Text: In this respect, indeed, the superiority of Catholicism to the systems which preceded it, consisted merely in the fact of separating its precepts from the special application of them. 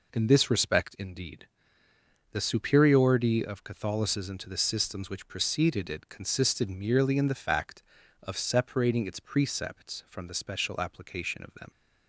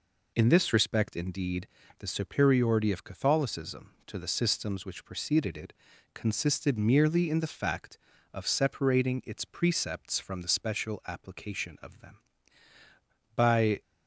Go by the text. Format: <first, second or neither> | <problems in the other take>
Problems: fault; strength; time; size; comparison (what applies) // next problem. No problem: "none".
first | goes on to say "By"; slight; from 13.3 s on; 0.46 s long